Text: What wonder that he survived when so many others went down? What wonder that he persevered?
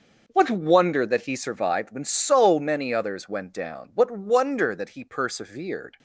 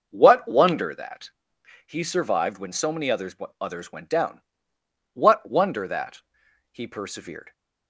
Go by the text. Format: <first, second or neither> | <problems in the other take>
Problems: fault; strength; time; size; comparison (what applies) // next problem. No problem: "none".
first | pauses between "that" and "he"; noticeable; at 1.3 s; 0.54 s long // says "others" twice; at 3.5 s // pauses between "that" and "he"; noticeable; at 6.2 s; 0.50 s long